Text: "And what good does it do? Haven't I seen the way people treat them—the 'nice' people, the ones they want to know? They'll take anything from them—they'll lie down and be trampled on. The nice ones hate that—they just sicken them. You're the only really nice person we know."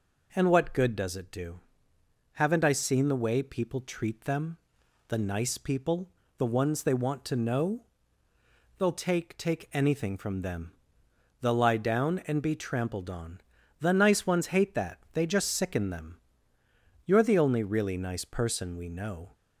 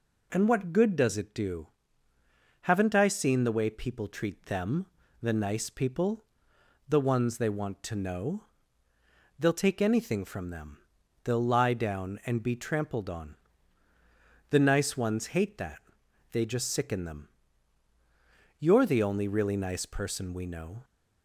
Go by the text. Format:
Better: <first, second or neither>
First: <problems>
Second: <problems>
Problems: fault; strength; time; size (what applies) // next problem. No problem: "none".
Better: second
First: says "take" twice; at 9.3 s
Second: none